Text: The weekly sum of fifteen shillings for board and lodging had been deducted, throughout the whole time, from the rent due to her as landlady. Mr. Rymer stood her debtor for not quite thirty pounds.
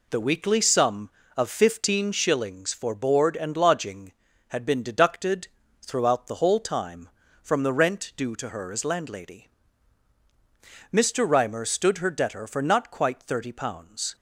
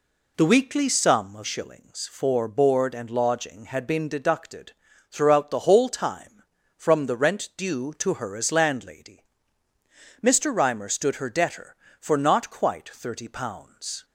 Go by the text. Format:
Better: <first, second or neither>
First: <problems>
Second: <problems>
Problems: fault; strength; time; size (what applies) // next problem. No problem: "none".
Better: first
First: none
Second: skips "fifteen"; at 1.4 s